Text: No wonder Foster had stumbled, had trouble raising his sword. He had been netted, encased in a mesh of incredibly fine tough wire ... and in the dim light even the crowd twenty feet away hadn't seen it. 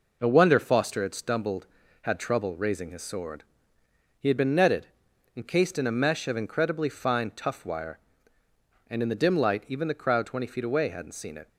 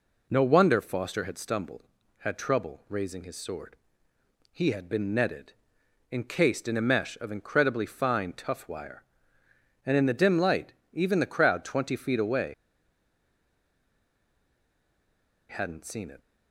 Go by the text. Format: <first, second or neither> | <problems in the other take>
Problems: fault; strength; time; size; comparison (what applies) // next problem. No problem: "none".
first | pauses between "light" and "even"; slight; at 10.7 s; 0.18 s long // pauses between "away" and "hadn't"; strong; at 12.5 s; 2.9 s long